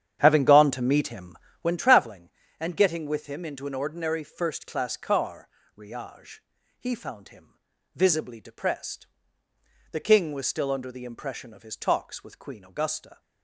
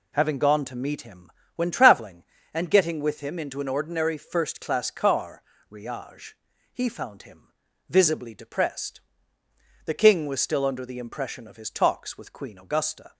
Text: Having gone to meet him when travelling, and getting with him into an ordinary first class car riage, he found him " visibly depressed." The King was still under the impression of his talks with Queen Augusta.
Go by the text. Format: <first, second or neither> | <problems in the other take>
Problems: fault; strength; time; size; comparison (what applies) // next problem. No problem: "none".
second | starts louder than the rest; strong; until 1.8 s; 9.5 dB // pauses between "him" and "when"; slight; at 1.3 s; 0.24 s long; slight in the second // pauses between "car" and "riage"; slight; at 5.4 s; 0.30 s long; slight in the second